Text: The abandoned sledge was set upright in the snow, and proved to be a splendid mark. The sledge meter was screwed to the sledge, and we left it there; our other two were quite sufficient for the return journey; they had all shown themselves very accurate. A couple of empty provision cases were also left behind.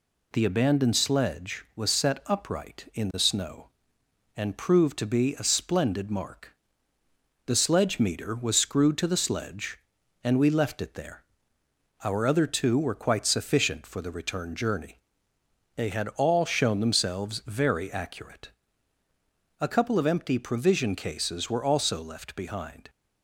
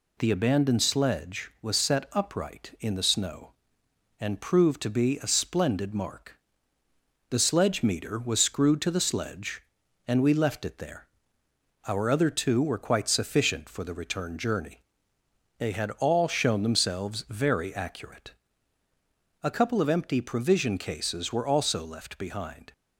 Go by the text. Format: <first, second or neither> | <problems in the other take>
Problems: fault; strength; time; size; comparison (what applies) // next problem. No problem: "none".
neither | none